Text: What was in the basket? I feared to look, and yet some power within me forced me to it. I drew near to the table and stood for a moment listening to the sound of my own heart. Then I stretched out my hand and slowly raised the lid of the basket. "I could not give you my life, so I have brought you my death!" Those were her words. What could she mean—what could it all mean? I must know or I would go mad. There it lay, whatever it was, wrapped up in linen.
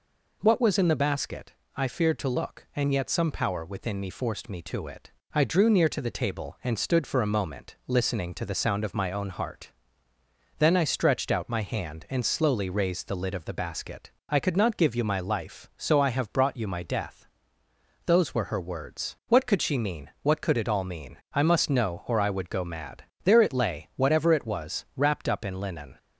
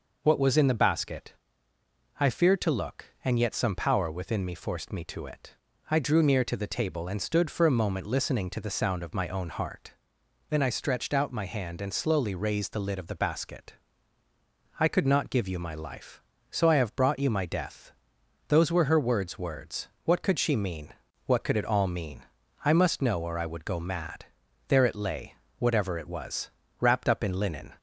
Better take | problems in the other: first | says "words" twice; at 19.3 s

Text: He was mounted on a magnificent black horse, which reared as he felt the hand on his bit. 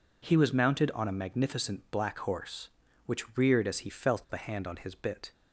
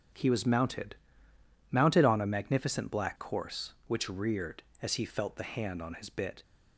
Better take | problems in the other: first | starts louder than the rest; strong; until 1.9 s; 7.5 dB // says "mounted" twice; at 1.7 s

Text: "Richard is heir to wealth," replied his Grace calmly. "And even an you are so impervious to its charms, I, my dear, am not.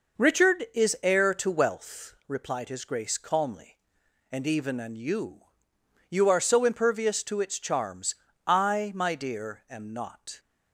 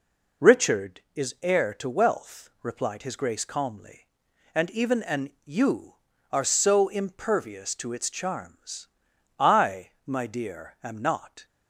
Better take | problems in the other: second | says "you" twice; at 6.0 s

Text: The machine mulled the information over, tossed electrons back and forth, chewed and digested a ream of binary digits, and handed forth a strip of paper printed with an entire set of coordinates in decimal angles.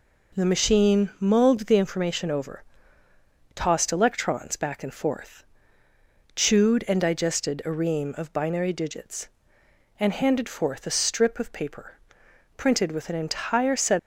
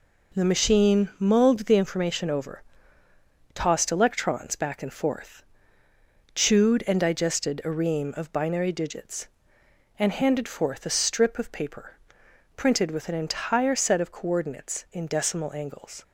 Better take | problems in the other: second | pauses between "paper" and "printed"; noticeable; at 11.9 s; 0.60 s long; noticeable in the second // stops before "of coordinates in decimal angles"; at 13.9 s

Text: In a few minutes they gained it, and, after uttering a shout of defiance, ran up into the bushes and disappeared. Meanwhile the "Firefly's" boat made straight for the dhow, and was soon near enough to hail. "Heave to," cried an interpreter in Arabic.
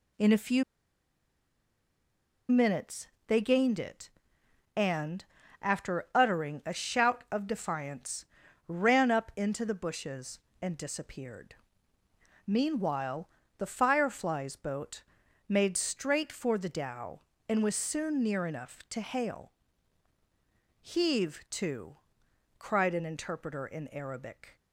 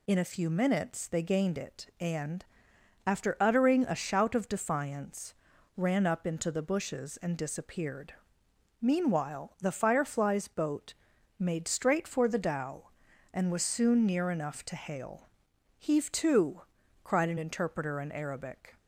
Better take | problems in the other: second | pauses between "few" and "minutes"; strong; at 0.6 s; 1.8 s long // pauses between "minutes" and "they"; slight; at 3.0 s; 0.20 s long // pauses between "Meanwhile" and "the"; slight; at 13.2 s; 0.30 s long // pauses between "boat" and "made"; noticeable; at 15.0 s; 0.48 s long; also in the second

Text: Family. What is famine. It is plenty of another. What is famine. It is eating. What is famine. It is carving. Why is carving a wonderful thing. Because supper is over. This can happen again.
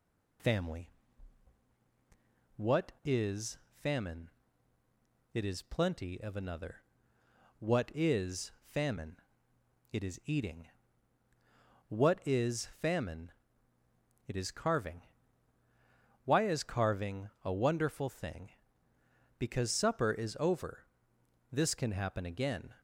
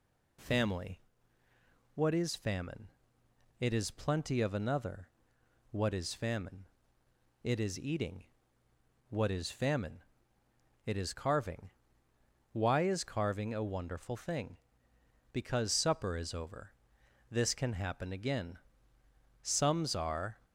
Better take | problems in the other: first | goes on to say "Sums are"; noticeable; from 19.4 s on; 0.96 s long

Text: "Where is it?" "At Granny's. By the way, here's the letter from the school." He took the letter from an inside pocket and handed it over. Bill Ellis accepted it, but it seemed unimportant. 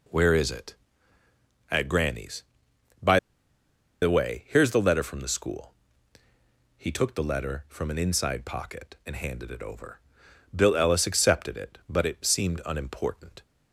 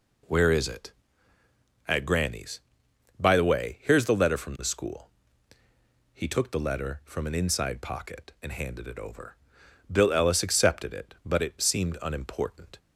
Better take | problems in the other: second | pauses between "By" and "the"; noticeable; at 3.1 s; 0.82 s long

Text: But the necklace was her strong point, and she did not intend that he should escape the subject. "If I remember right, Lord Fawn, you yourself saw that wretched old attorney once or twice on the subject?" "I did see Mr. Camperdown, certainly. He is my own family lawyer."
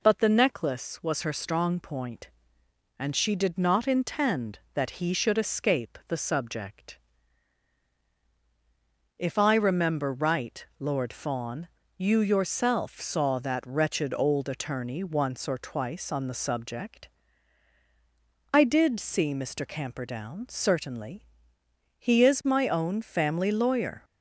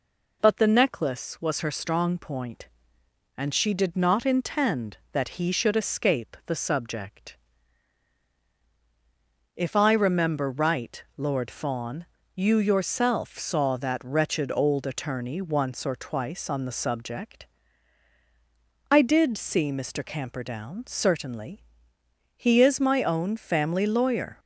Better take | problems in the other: neither | none

